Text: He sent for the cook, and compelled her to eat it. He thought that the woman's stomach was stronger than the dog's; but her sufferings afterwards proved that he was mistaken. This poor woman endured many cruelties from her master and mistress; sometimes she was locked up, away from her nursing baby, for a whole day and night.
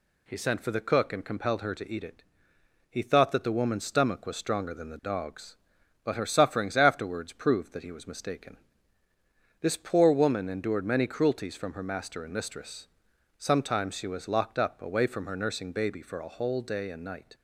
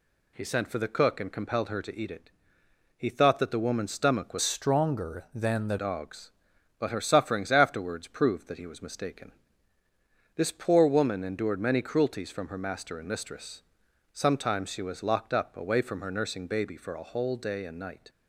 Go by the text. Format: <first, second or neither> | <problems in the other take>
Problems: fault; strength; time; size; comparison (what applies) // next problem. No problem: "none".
first | changes voice from "stronger" to "the"; from 4.4 to 5.7 s; 1.3 s long